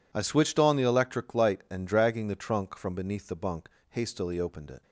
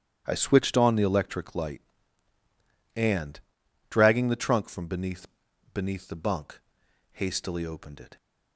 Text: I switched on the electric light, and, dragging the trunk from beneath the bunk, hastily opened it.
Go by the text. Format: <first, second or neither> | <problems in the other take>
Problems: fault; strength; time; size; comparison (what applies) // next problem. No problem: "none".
first | starts louder than the rest; strong; until 1.2 s; 10.5 dB // says "beneath" twice; at 5.7 s